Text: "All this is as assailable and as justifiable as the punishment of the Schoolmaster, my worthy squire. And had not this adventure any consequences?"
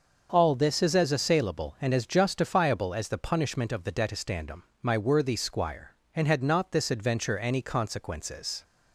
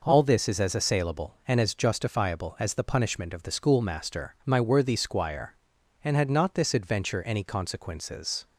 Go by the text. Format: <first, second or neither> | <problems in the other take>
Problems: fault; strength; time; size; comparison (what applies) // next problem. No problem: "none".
second | starts louder than the rest; until 1.3 s; 6.5 dB // says "Detestandum" for "Schoolmaster"; at 3.9 s